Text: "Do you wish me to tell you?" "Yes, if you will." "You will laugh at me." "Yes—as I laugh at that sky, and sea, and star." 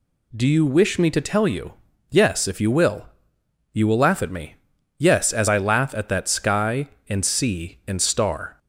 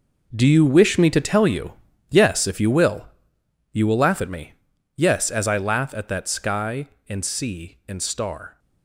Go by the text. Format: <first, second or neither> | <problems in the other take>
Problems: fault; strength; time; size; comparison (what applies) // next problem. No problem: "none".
first | gets quieter; strong; throughout; 13 dB